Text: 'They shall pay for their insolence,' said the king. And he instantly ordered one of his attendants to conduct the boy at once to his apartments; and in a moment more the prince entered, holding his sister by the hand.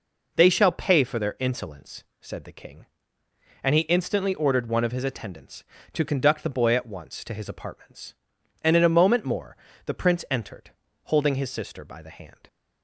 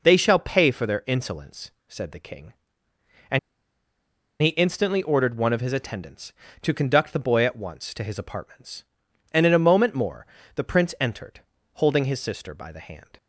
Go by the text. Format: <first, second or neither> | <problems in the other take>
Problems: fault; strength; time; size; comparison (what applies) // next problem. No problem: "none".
first | pauses between "And" and "he"; at 3.3 s; 1.0 s long // pauses between "more" and "the"; slight; at 10.2 s; 0.30 s long; slight in the first